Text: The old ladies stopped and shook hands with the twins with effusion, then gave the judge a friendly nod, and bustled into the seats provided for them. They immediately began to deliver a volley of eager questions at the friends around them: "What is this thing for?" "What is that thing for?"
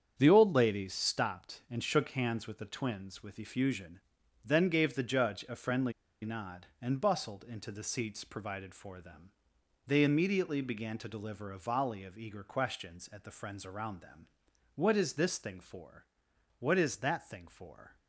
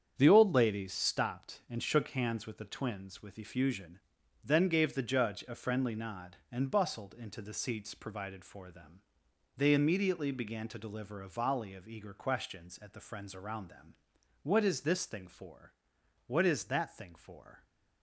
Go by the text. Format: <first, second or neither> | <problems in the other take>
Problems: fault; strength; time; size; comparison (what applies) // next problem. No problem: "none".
second | starts louder than the rest; strong; until 1.2 s; 8 dB; strong in the second // pauses between "friendly" and "nod"; slight; at 5.9 s; 0.31 s long